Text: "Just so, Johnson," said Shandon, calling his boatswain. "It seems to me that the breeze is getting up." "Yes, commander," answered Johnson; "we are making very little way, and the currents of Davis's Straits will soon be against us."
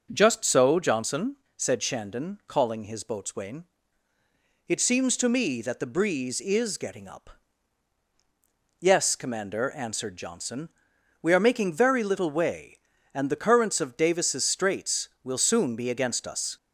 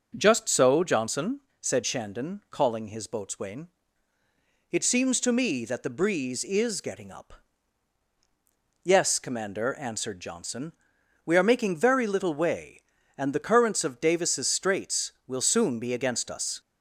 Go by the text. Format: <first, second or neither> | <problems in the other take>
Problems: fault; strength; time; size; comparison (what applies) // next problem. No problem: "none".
neither | none